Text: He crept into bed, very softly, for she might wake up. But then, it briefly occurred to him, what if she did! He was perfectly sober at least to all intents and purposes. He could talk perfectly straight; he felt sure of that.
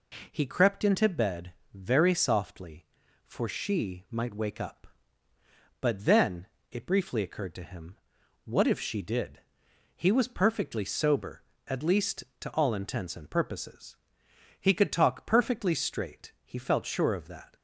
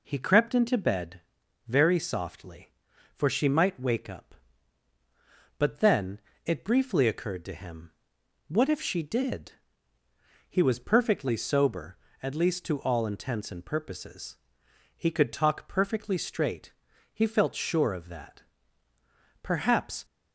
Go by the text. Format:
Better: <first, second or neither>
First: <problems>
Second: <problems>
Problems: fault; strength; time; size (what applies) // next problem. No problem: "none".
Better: first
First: none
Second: goes on to say "Perhaps"; noticeable; from 19.4 s on; 0.64 s long